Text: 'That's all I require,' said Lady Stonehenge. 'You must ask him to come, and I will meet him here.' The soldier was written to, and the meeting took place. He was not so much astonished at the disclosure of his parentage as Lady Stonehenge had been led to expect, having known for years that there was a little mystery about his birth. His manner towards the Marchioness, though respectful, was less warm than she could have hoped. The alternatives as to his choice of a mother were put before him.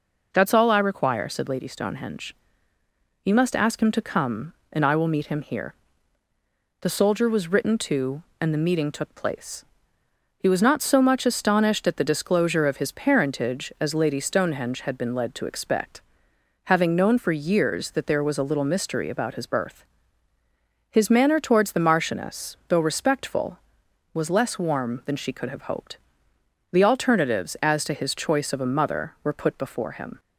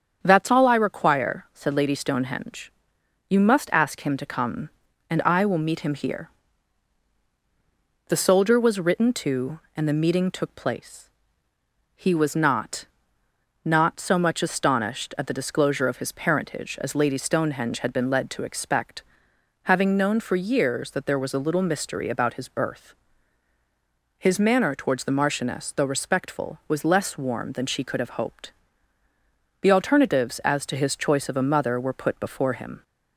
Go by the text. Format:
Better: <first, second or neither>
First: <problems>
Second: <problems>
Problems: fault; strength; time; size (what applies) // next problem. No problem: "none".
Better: first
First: none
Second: starts louder than the rest; strong; until 1.2 s; 7.5 dB // says "not" twice; at 13.6 s